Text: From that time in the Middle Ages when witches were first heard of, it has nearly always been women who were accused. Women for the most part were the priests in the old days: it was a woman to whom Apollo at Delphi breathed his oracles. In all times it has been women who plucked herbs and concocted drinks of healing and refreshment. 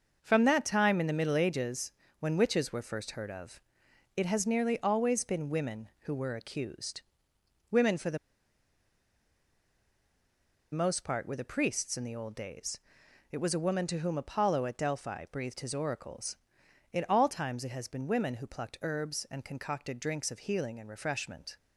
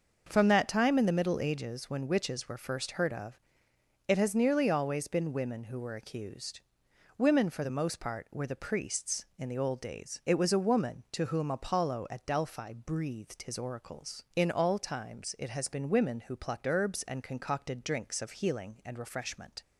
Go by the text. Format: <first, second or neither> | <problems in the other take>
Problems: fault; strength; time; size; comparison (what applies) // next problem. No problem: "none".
second | starts louder than the rest; until 1.2 s; 6.5 dB; also in the second // pauses between "Ages" and "when"; slight; at 1.9 s; 0.28 s long // pauses between "the" and "most"; strong; at 8.1 s; 2.5 s long